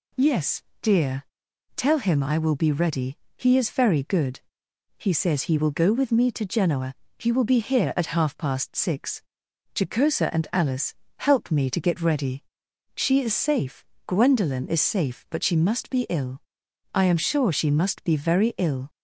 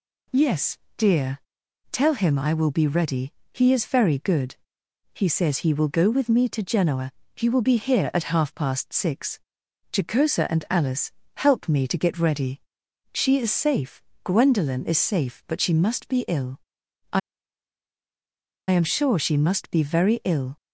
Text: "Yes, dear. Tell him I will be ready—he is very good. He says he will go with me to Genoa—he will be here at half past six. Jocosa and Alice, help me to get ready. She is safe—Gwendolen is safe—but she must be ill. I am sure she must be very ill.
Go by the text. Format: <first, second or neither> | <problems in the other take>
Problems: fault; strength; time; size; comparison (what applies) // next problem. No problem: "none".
first | pauses between "I" and "am"; strong; at 17.1 s; 1.5 s long